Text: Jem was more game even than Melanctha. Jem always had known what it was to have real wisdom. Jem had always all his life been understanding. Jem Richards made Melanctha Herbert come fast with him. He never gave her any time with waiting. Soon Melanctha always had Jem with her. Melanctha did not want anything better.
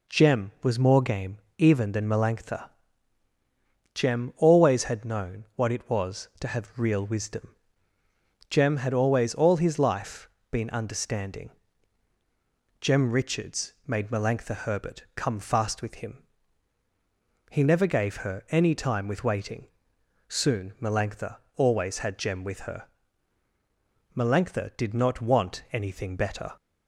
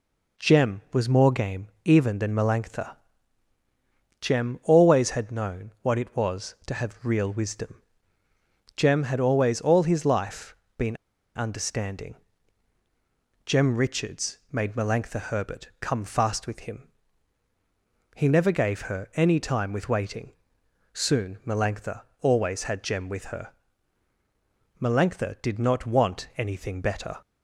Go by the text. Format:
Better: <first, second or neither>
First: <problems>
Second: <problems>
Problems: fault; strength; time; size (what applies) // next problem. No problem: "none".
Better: first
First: pauses between "game" and "even"; slight; at 1.3 s; 0.20 s long // pauses between "life" and "been"; slight; at 10.2 s; 0.22 s long // pauses between "Melanctha" and "always"; slight; at 21.3 s; 0.18 s long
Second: pauses between "game" and "even"; slight; at 1.6 s; 0.16 s long // pauses between "life" and "been"; slight; at 10.5 s; 0.22 s long // pauses between "been" and "understanding"; at 10.9 s; 0.38 s long // pauses between "Melanctha" and "always"; slight; at 22.0 s; 0.18 s long